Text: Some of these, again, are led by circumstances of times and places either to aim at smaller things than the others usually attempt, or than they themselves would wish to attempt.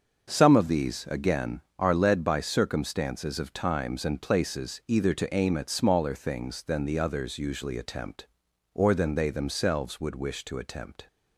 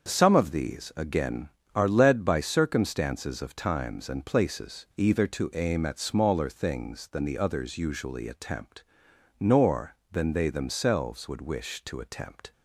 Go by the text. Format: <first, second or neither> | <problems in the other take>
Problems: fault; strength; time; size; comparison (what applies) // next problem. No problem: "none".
first | starts louder than the rest; until 1.0 s; 6.5 dB; also in the first // says "nor" for "or"; at 9.3 s